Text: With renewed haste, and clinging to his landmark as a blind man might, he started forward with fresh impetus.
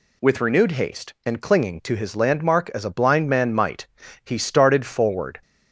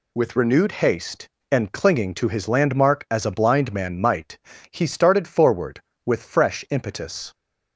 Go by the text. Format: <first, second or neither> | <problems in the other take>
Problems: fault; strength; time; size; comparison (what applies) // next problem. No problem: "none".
second | stops before "with fresh impetus"; at 5.4 s